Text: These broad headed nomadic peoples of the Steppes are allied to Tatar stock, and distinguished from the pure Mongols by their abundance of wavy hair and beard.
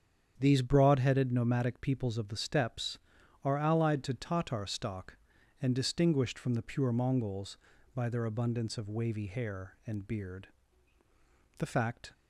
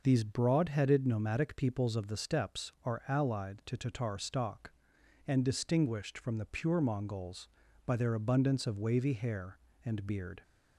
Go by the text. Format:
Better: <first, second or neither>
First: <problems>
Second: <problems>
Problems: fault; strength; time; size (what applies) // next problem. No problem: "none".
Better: second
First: starts louder than the rest; strong; until 1.3 s; 8 dB // goes on to say "The fact"; from 11.5 s on; 0.56 s long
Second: none